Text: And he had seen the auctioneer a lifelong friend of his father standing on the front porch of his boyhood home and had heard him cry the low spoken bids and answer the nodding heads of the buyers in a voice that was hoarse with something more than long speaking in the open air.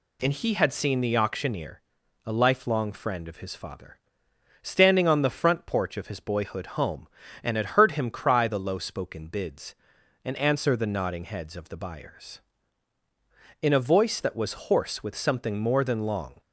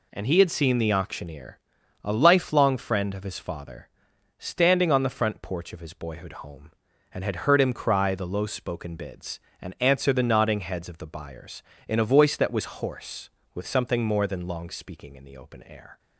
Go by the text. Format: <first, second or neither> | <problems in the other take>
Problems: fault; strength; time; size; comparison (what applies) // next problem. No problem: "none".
second | pauses between "auctioneer" and "a"; noticeable; at 1.8 s; 0.46 s long; also in the second // pauses between "father" and "standing"; noticeable; at 3.9 s; 0.66 s long; noticeable in the second // stops before "speaking in the open air"; at 16.3 s